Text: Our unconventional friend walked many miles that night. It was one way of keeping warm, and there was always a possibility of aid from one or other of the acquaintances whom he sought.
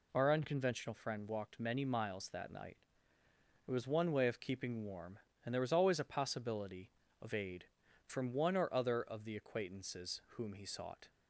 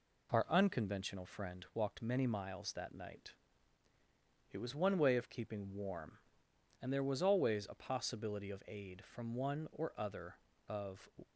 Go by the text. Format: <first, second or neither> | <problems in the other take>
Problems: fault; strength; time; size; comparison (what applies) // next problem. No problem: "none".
first | stops before "the acquaintances whom he sought"; at 11.2 s